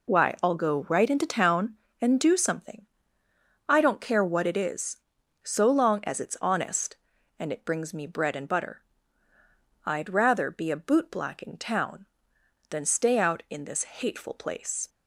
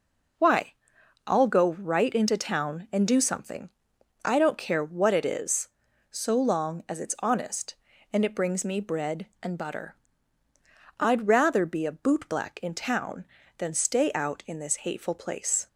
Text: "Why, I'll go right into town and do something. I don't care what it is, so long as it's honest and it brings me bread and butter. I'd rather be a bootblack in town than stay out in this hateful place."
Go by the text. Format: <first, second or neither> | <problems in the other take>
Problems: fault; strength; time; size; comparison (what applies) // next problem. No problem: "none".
neither | none